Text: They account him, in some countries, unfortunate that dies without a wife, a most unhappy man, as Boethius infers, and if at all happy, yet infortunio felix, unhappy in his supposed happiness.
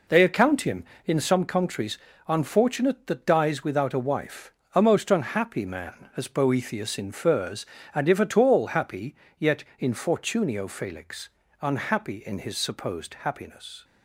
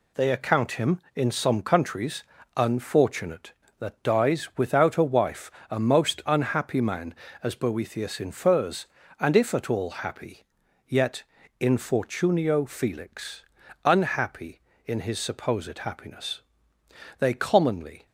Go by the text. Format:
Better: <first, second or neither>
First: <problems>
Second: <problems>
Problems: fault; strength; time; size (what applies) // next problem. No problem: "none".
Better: first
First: pauses between "yet" and "infortunio"; slight; at 9.6 s; 0.16 s long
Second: pauses between "yet" and "infortunio"; slight; at 11.2 s; 0.36 s long // goes on to say "They commonly"; noticeable; from 17.1 s on; 0.86 s long